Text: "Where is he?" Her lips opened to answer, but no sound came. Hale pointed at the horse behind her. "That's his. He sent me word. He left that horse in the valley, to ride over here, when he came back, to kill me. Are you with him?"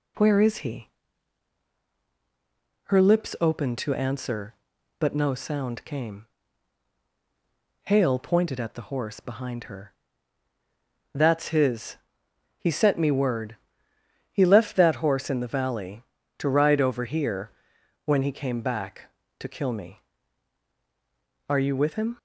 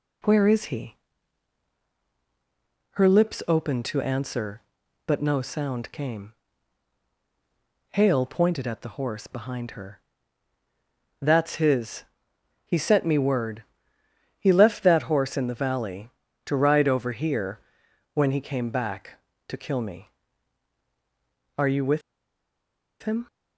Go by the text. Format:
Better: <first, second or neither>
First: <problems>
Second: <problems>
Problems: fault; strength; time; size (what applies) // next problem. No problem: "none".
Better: first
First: none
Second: pauses between "with" and "him"; at 22.0 s; 1.0 s long